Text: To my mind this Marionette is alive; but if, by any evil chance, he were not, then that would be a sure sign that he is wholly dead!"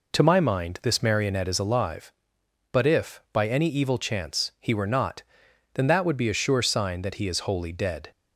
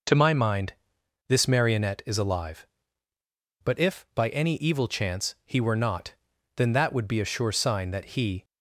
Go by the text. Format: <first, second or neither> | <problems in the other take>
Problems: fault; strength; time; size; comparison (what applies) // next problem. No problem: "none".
first | pauses between "mind" and "this"; noticeable; at 0.7 s; 0.54 s long // stops before "is wholly dead"; at 8.4 s